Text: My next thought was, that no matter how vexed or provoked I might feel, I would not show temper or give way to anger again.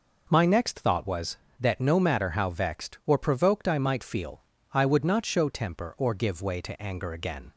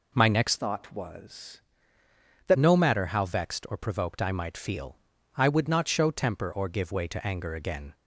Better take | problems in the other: first | changes voice from "thought" to "that"; from 0.5 to 2.5 s; 2.0 s long

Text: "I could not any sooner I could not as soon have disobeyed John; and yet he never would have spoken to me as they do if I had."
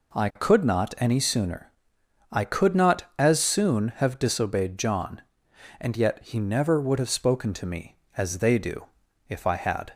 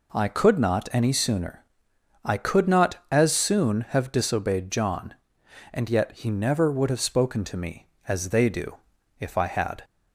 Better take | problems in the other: neither | pauses between "sooner" and "I"; noticeable; the same in both // pauses between "do" and "if"; the same in both

